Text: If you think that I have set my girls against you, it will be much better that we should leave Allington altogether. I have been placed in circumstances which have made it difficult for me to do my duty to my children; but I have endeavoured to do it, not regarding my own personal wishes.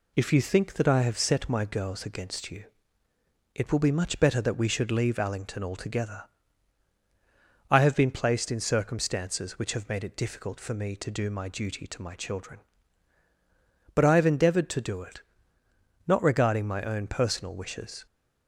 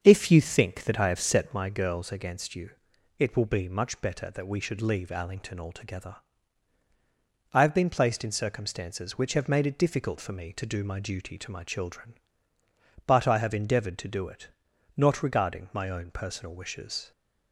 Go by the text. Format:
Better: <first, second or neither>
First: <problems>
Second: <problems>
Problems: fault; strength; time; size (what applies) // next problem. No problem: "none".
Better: first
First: none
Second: starts louder than the rest; until 1.7 s; 7 dB